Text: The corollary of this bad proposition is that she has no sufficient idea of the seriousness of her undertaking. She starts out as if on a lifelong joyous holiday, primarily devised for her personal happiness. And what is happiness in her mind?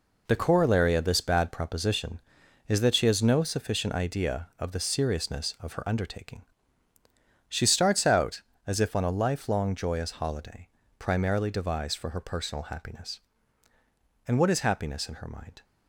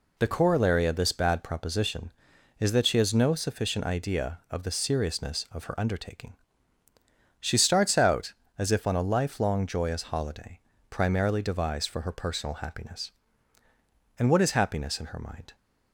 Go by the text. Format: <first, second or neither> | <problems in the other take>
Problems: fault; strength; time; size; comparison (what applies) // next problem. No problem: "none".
second | gets quieter; strong; throughout; 9.5 dB